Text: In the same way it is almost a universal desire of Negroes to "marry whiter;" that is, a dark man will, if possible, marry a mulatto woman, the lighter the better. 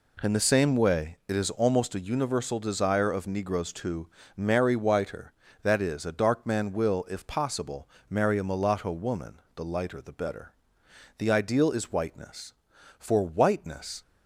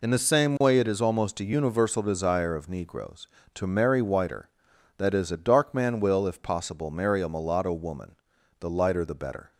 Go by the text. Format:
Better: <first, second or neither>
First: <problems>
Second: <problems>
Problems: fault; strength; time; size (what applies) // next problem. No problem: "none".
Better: second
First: pauses between "to" and "marry"; slight; at 4.0 s; 0.28 s long // goes on to say "The ideal is whiteness for whiteness"; strong; from 11.1 s on; 2.8 s long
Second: none